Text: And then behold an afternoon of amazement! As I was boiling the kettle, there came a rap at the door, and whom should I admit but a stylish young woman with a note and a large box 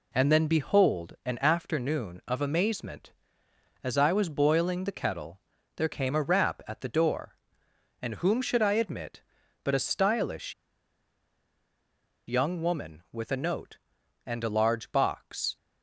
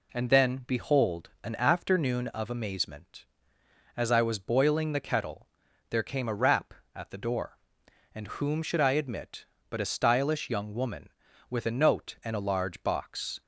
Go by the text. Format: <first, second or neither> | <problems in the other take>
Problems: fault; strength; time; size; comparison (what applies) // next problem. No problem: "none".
second | pauses between "stylish" and "young"; strong; at 10.5 s; 1.7 s long